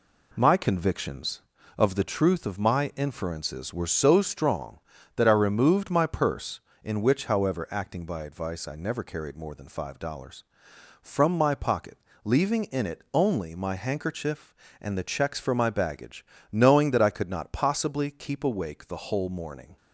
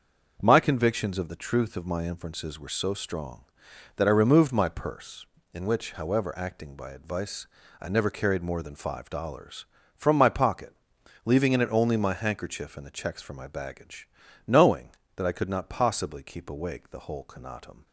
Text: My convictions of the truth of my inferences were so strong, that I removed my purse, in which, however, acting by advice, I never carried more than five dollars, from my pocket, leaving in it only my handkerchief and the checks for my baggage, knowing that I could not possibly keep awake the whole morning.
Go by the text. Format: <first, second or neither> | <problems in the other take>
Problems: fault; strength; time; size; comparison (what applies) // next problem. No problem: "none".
first | starts louder than the rest; until 1.4 s; 6.5 dB // says "conatum" for "morning"; at 17.2 s